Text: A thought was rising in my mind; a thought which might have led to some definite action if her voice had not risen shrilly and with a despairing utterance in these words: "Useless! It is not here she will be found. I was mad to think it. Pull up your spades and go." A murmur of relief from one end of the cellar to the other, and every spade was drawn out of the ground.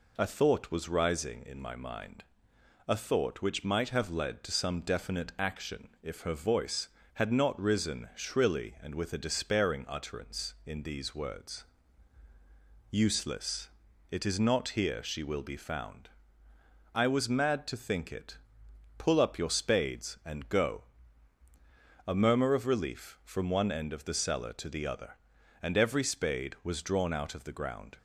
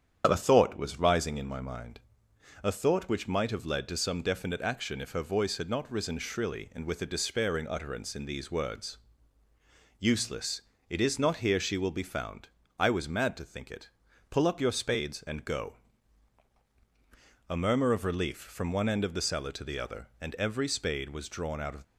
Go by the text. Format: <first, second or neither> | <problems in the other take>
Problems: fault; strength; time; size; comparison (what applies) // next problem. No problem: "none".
first | starts louder than the rest; strong; until 1.3 s; 8.5 dB // stops before "the ground"; at 21.8 s